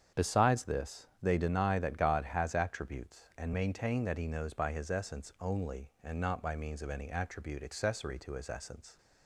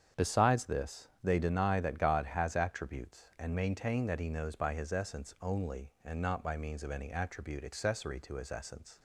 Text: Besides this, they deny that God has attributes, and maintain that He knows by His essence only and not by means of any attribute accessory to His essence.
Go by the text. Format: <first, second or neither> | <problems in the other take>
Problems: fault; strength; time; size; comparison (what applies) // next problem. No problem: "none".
neither | starts louder than the rest; strong; the same in both